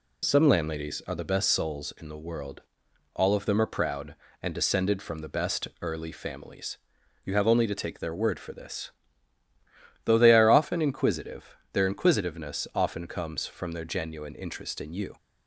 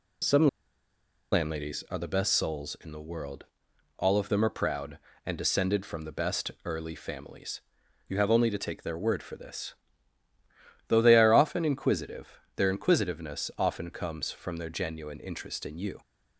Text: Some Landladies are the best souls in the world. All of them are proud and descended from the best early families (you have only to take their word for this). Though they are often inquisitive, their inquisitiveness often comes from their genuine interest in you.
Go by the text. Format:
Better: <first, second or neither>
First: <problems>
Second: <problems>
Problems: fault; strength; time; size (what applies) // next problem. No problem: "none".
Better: first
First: pauses between "best" and "early"; slight; at 5.6 s; 0.16 s long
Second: pauses between "Some" and "Landladies"; noticeable; at 0.4 s; 0.85 s long // pauses between "best" and "early"; slight; at 6.4 s; 0.16 s long